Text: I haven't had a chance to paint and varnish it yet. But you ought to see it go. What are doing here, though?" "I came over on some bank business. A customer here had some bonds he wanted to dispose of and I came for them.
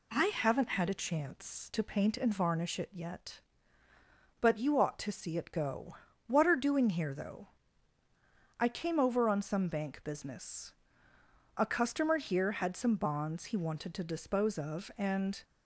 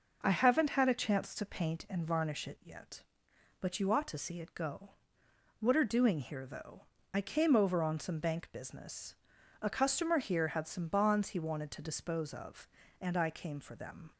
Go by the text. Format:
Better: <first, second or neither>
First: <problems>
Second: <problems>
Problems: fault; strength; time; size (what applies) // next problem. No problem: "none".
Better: second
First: stops before "I came for them"; at 15.4 s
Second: none